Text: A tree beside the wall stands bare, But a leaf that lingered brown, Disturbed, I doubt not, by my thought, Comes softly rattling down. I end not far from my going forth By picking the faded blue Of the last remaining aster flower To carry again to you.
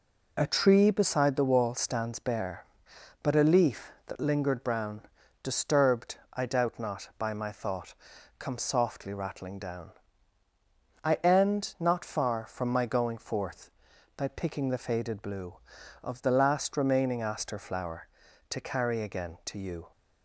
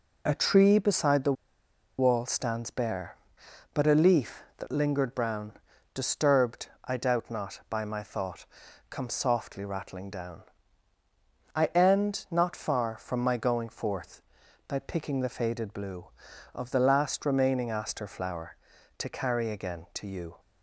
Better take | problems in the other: first | pauses between "the" and "wall"; noticeable; at 1.3 s; 0.66 s long

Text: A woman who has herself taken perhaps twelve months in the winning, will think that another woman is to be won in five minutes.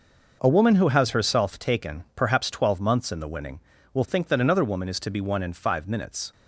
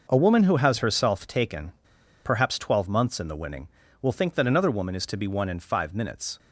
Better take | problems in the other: first | pauses between "taken" and "perhaps"; noticeable; at 1.7 s; 0.53 s long

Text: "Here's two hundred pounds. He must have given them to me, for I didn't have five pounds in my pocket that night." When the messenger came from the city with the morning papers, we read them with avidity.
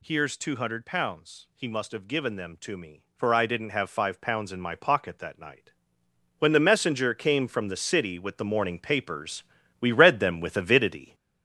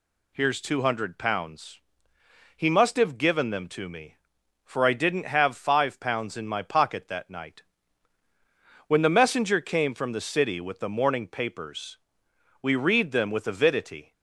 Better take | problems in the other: second | gets louder; noticeable; throughout; 5.5 dB

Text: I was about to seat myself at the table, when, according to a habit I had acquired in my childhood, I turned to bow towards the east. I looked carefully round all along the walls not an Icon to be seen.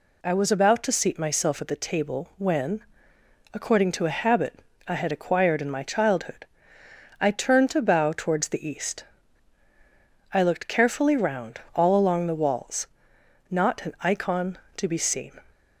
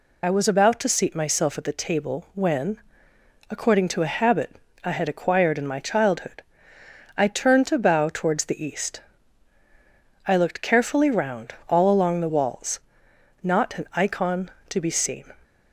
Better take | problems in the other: first | loses the start of "I"; at 0.2 s; 40 ms // pauses between "habit" and "I"; slight; at 4.5 s; 0.28 s long; slight in the first // pauses between "walls" and "not"; noticeable; at 12.7 s; 0.66 s long; noticeable in the first

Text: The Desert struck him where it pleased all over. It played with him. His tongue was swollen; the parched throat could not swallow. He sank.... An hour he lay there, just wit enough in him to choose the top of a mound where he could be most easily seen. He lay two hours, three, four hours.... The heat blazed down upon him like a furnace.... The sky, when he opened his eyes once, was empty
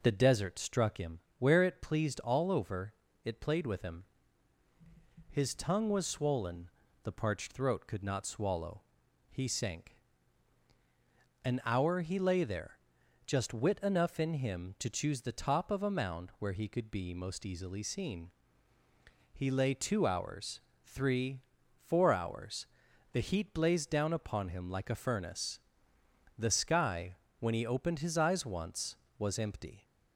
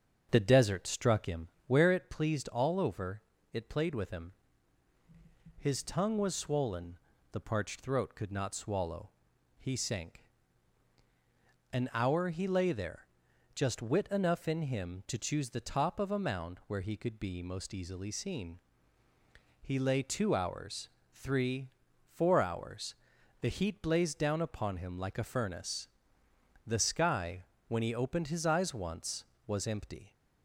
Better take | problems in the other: first | starts louder than the rest; until 1.8 s; 7 dB // pauses between "him" and "where"; slight; at 1.4 s; 0.18 s long; slight in the first

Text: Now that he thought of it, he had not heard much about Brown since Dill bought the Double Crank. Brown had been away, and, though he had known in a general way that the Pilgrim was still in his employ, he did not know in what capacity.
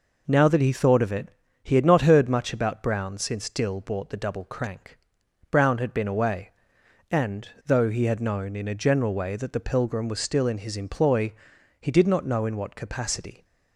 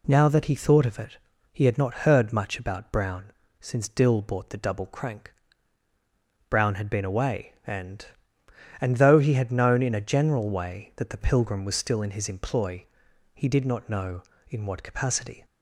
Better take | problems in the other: first | pauses between "Brown" and "since"; slight; at 3.3 s; 0.28 s long // says "and" twice; at 8.7 s

